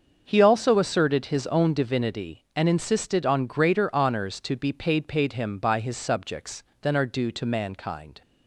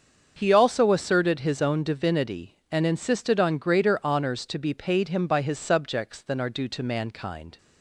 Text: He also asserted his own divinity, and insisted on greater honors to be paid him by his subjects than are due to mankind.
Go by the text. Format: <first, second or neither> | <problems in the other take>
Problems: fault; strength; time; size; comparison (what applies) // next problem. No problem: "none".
second | starts louder than the rest; until 1.2 s; 6.5 dB; also in the second // says "paid" twice; at 5.0 s